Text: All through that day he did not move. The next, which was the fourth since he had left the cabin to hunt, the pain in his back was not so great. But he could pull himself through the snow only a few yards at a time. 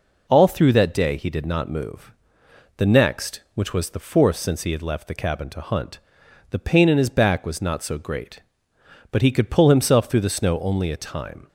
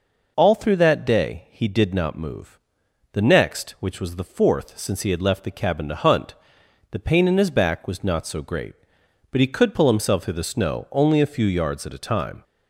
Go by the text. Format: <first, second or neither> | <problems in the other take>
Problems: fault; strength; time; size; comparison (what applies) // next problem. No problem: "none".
second | skips "few yards at a"; at 10.9 s